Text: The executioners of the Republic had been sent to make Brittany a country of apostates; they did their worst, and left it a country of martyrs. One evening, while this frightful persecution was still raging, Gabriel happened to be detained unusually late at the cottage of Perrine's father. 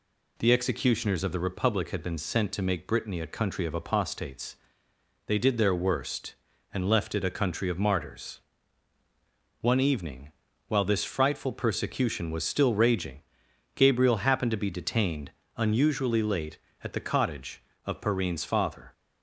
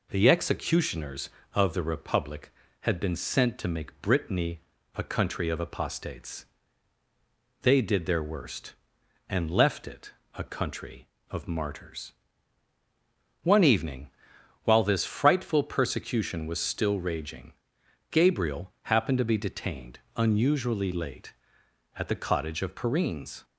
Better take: first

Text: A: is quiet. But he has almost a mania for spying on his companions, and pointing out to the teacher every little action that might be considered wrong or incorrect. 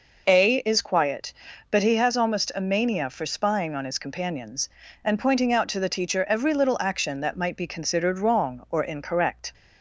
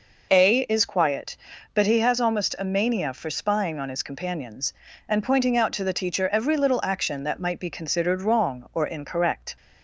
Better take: neither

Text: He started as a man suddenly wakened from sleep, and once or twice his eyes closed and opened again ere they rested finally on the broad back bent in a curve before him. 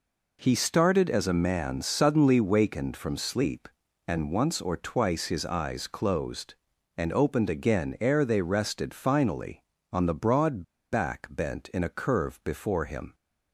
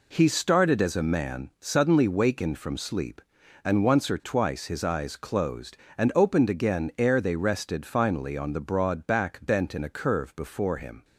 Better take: second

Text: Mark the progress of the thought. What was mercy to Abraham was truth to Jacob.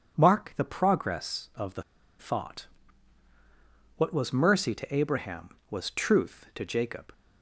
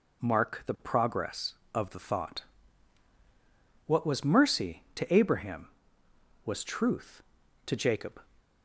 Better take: second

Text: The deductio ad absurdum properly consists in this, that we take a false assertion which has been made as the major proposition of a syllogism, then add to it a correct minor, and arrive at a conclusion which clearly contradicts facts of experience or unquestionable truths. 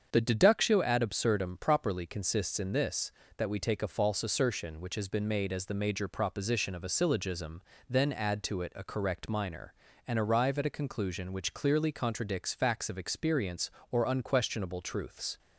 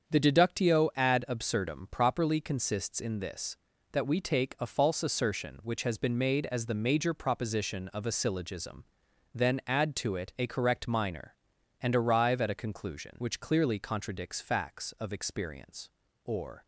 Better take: first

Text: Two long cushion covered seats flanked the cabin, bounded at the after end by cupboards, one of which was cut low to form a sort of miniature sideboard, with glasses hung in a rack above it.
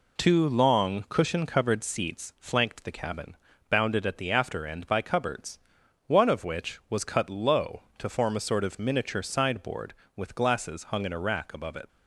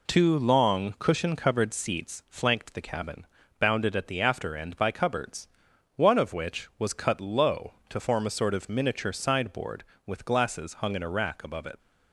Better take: neither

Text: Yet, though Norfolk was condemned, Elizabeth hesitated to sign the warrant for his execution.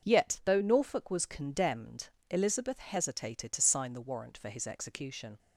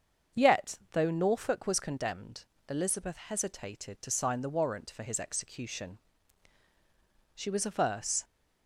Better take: first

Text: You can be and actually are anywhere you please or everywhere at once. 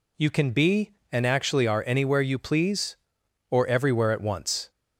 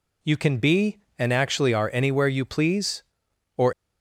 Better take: first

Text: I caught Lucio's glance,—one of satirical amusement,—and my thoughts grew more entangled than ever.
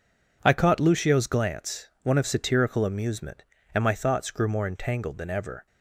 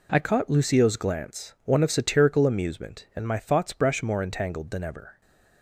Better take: first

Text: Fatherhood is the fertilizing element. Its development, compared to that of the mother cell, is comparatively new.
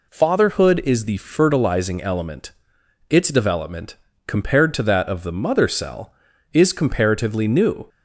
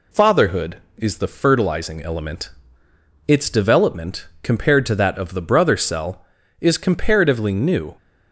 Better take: first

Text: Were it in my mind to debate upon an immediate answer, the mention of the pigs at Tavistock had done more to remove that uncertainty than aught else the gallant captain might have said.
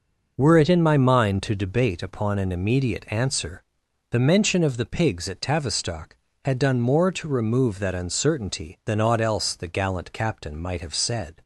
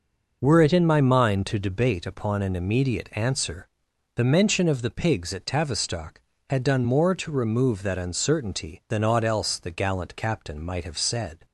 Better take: neither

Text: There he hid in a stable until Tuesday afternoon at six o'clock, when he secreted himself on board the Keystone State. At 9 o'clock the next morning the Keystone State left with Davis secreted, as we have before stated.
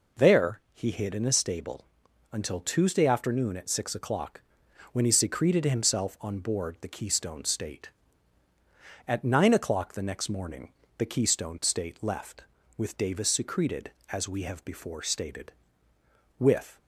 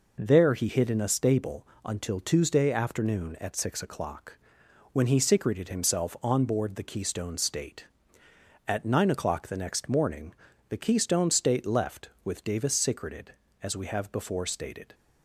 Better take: second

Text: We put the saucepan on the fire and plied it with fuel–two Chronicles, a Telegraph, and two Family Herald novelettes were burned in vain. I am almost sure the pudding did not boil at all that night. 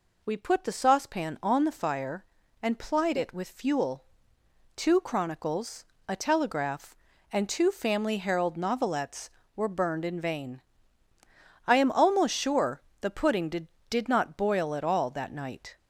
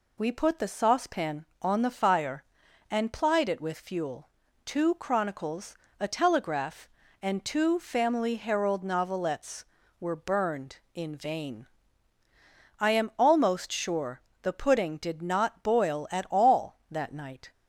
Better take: second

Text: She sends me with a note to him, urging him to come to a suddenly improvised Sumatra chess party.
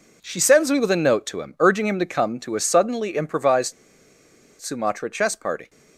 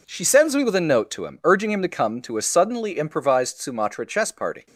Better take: second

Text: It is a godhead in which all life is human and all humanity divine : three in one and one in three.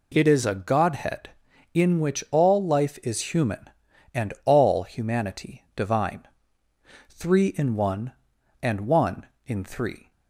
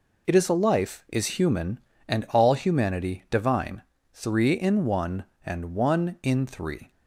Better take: first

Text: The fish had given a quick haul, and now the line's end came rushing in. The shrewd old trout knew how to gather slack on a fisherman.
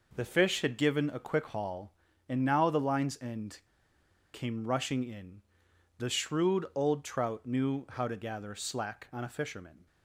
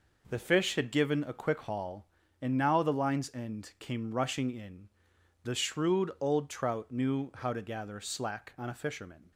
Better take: second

